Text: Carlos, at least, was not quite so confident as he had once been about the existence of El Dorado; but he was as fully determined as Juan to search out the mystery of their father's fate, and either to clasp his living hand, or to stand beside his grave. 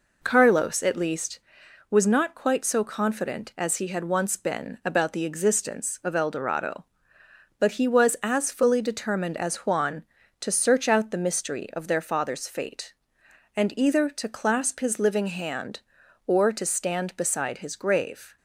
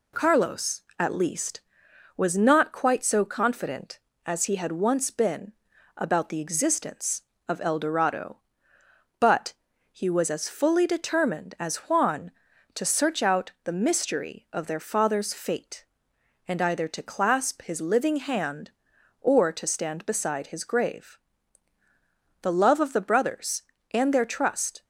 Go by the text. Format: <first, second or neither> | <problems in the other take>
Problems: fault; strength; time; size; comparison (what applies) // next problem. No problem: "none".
first | pauses between "been" and "about"; at 5.5 s; 0.44 s long // pauses between "but" and "he"; slight; at 9.5 s; 0.36 s long // goes on to say "The love of the brothers and their trust"; strong; from 22.4 s on; 2.4 s long